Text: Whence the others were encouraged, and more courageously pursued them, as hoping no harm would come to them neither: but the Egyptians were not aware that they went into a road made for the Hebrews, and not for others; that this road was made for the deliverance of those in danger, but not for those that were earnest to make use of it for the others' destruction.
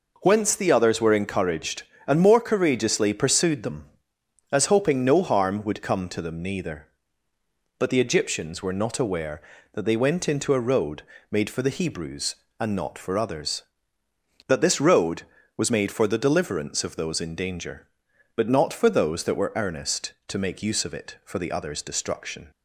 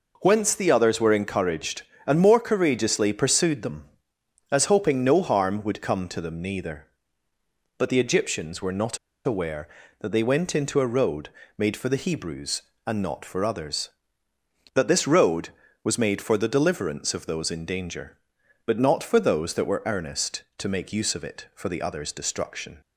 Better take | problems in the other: first | pauses between "not" and "aware"; slight; at 8.9 s; 0.27 s long // pauses between "road" and "made"; slight; at 11.2 s; 0.28 s long; slight in the first

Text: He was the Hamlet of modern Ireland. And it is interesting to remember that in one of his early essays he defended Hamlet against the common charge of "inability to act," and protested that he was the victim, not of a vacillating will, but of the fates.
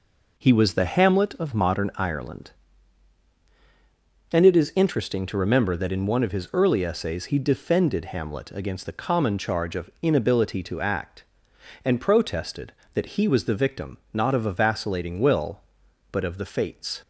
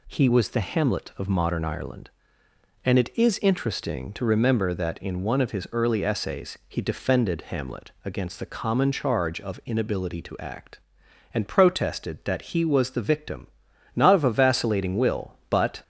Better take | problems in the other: first | stops before "of the fates"; at 15.8 s

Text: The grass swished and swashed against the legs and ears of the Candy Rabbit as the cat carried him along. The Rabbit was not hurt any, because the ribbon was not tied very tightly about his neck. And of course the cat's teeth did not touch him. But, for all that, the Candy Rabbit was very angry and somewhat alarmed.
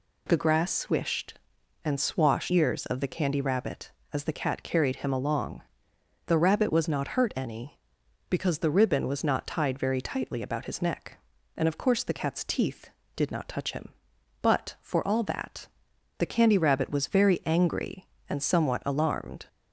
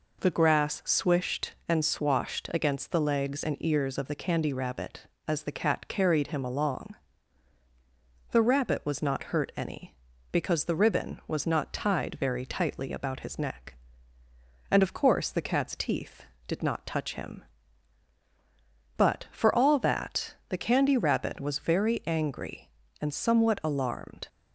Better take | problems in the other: second | skips "against the legs and"; at 2.5 s

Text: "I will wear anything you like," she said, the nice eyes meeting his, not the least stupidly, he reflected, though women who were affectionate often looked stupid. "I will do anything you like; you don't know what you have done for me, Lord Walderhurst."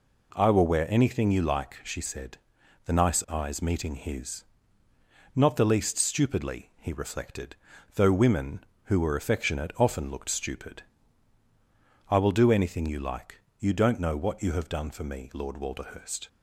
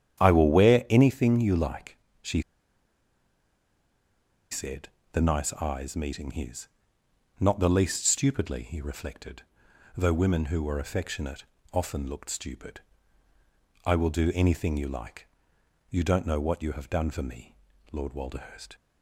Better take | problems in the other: first | starts louder than the rest; strong; until 1.2 s; 9.5 dB // pauses between "she" and "said"; strong; at 2.4 s; 2.1 s long // pauses between "affectionate" and "often"; slight; at 11.4 s; 0.28 s long

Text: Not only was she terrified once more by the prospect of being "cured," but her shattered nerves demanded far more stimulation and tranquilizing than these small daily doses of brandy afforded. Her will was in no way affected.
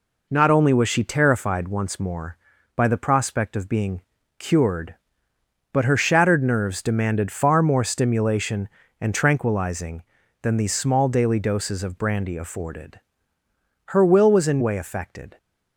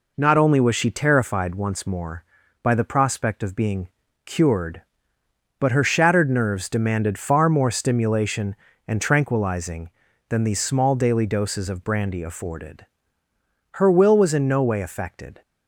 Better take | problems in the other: second | pauses between "being" and "cured"; at 4.0 s; 0.38 s long; also in the second // skips "no"; at 14.6 s

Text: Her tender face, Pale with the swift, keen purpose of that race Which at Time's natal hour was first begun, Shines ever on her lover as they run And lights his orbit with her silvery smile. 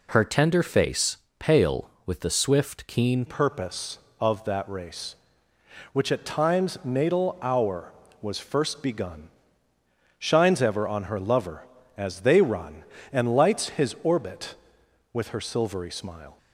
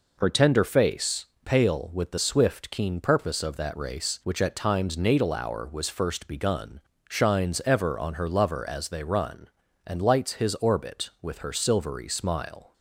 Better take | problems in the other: second | changes voice at "purpose"; from 3.2 s on; 13.1 s long

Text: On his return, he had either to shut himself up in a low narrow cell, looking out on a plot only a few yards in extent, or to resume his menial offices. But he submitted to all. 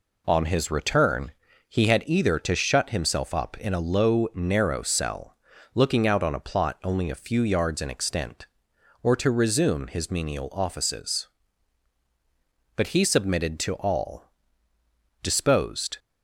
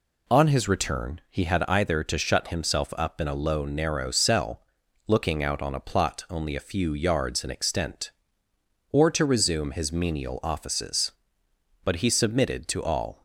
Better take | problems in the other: second | goes on to say "Disposed"; noticeable; from 15.2 s on; 0.76 s long

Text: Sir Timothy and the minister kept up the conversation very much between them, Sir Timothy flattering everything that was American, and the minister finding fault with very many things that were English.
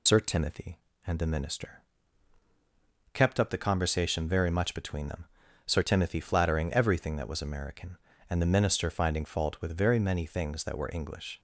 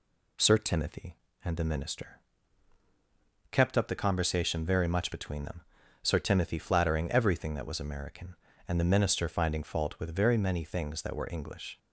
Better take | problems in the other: second | loses the start of "Sir"; at 0.0 s; 60 ms // pauses between "minister" and "kept"; strong; at 1.8 s; 1.3 s long; strong in the second

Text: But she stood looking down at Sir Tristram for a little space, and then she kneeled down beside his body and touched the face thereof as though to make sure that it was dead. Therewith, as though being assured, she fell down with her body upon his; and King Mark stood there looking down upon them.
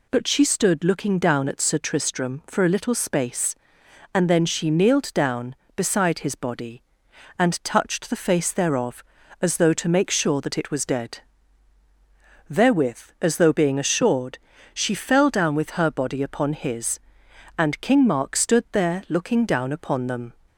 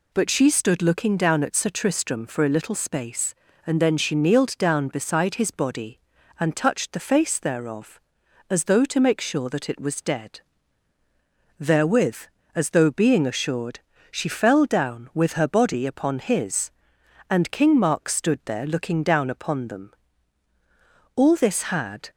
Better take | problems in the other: first | goes on to say "All this had"; noticeable; from 21.1 s on; 0.94 s long

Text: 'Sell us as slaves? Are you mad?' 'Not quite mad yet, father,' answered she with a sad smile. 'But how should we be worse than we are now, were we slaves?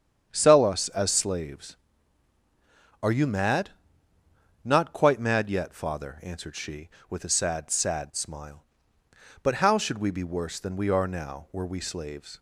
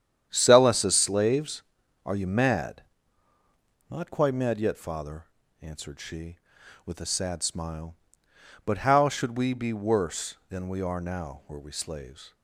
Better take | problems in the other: second | starts louder than the rest; strong; until 1.3 s; 8 dB; strong in the second // says "sad" twice; at 7.7 s

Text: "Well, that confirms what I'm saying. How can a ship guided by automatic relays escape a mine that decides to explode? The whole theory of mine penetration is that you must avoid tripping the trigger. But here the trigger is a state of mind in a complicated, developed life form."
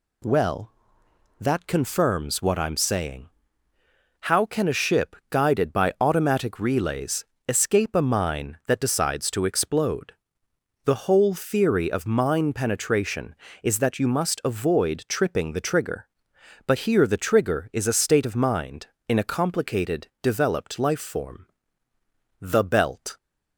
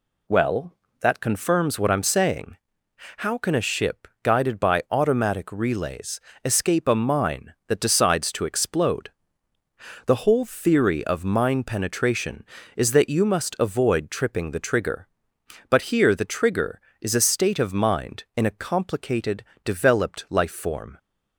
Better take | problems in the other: second | pauses between "relays" and "escape"; slight; at 7.2 s; 0.24 s long; slight in the second // goes on to say "The belt"; noticeable; from 22.4 s on; 0.76 s long

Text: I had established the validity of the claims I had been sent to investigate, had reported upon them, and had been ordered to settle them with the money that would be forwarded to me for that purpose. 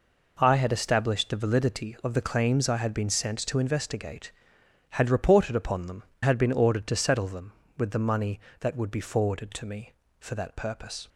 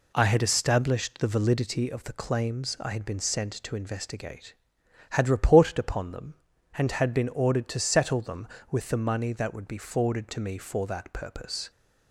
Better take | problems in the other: second | skips "and"; at 6.1 s

